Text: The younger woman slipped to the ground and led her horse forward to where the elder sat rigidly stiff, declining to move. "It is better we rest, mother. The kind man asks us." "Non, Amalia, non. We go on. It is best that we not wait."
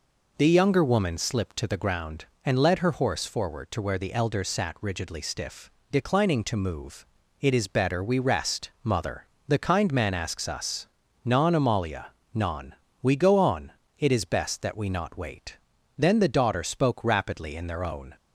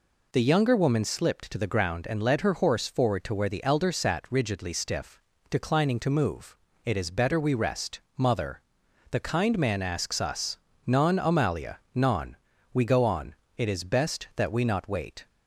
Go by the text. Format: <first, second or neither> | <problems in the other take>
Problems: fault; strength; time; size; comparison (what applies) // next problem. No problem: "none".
second | goes on to say "Then the daughter spoke rapidly in their own"; strong; from 15.9 s on; 2.1 s long